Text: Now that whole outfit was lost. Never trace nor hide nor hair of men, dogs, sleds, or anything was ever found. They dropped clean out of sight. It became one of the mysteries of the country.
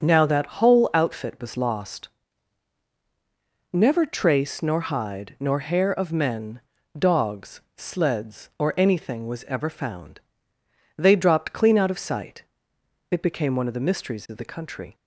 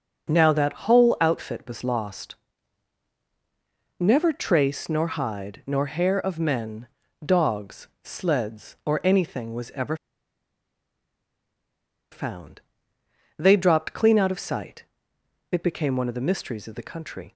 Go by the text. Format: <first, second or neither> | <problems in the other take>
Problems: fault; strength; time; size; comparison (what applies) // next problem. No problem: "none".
first | starts louder than the rest; until 1.3 s; 6.5 dB; also in the first // pauses between "ever" and "found"; strong; at 9.9 s; 2.1 s long